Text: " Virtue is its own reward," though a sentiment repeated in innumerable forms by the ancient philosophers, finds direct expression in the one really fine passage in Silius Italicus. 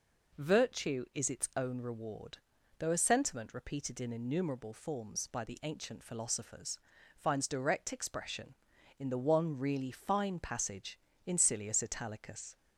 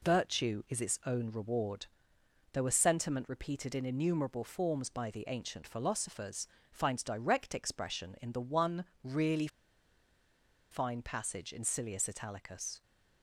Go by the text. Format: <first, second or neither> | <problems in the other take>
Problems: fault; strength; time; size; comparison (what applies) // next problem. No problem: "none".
first | pauses between "one" and "really"; slight; at 8.8 s; 0.18 s long // pauses between "really" and "fine"; at 9.4 s; 1.2 s long